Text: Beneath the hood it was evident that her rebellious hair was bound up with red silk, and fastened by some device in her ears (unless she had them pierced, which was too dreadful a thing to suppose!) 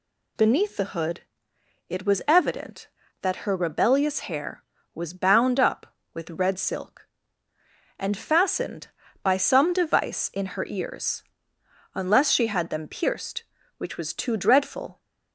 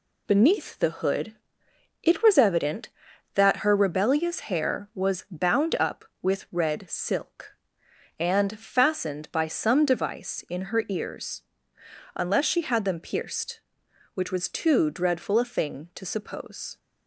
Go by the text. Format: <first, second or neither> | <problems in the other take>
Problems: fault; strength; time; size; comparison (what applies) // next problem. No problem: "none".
second | pauses between "hood" and "it"; noticeable; at 1.2 s; 0.66 s long; noticeable in the second // stops before "a thing to suppose"; at 14.9 s